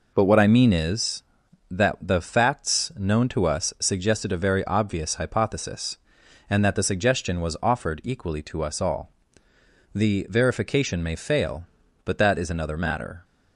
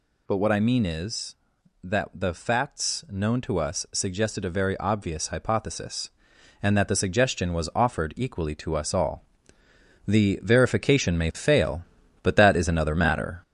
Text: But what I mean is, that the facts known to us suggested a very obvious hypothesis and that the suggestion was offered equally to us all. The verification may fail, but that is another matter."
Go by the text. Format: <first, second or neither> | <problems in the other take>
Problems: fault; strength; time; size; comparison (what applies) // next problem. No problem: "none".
first | gets louder; noticeable; throughout; 4.5 dB